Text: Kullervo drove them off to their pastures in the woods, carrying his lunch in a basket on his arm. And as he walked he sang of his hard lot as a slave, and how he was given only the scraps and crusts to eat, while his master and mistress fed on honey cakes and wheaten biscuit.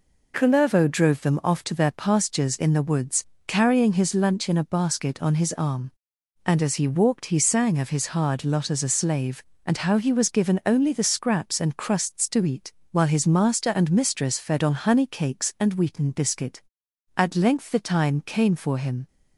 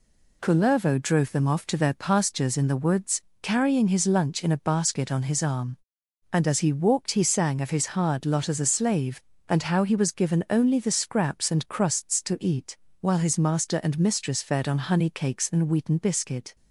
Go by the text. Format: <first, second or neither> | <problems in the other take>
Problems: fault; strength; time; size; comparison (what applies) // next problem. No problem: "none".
second | goes on to say "At length the time came for him"; strong; from 17.1 s on; 1.9 s long